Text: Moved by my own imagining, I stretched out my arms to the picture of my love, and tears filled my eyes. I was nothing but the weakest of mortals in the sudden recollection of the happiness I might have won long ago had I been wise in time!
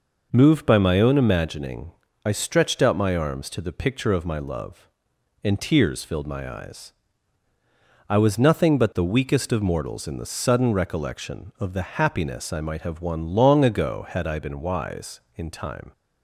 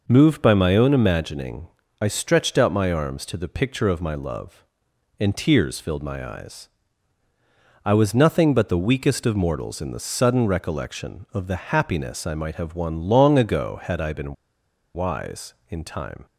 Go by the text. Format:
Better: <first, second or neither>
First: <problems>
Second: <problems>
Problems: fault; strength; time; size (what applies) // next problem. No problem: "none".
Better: first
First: none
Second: pauses between "been" and "wise"; noticeable; at 14.3 s; 0.60 s long